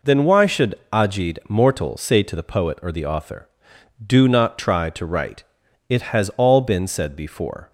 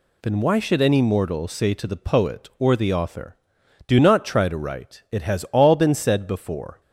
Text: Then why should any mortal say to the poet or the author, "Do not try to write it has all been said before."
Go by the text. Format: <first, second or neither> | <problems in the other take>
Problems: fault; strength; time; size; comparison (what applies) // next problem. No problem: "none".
second | says "ajid" for "any"; at 0.9 s // pauses between "write" and "it"; noticeable; at 5.4 s; 0.46 s long